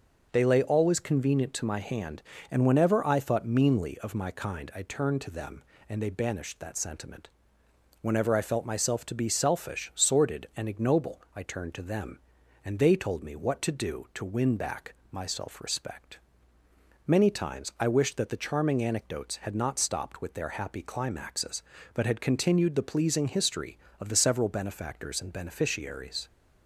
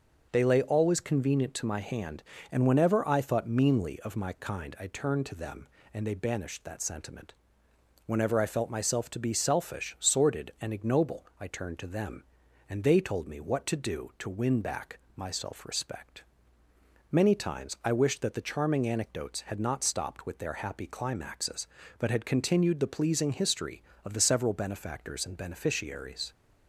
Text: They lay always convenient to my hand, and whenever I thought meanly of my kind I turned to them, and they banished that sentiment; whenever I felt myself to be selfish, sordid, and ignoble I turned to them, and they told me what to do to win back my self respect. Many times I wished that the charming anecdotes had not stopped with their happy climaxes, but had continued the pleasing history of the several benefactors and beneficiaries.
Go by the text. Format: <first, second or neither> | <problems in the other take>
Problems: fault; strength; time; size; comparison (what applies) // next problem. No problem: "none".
neither | pauses between "back" and "my"; slight; the same in both